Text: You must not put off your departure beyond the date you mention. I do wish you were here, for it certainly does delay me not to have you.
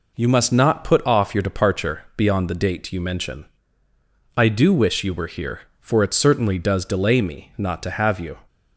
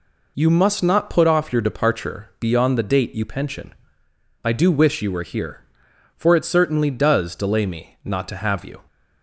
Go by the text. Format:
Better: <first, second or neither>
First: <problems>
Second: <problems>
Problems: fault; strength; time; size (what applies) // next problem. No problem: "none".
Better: first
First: none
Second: says "pension" for "mention"; at 3.2 s